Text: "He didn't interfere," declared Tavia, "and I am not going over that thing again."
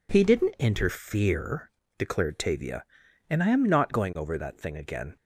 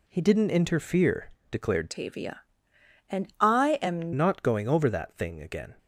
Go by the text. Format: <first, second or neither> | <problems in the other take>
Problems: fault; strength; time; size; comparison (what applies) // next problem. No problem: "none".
first | changes voice from "Tavia" to "am"; from 1.8 to 4.1 s; 2.3 s long